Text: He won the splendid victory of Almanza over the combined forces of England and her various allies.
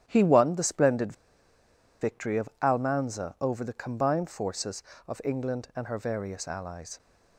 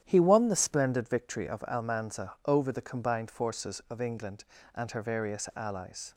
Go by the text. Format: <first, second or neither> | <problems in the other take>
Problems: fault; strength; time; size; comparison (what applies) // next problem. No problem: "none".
second | starts louder than the rest; strong; until 1.0 s; 11 dB; strong in the second // pauses between "splendid" and "victory"; noticeable; at 1.1 s; 0.89 s long